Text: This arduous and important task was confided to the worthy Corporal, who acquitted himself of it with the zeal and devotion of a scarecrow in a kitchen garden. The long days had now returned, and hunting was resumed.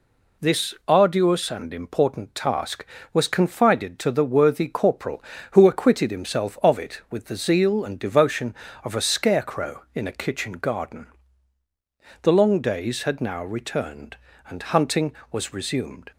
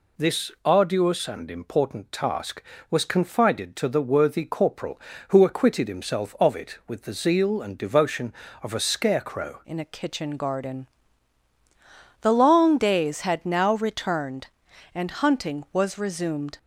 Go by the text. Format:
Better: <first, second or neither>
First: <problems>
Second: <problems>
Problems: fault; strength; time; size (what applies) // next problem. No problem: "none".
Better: first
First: none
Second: changes voice at "in"; from 9.6 s on; 6.9 s long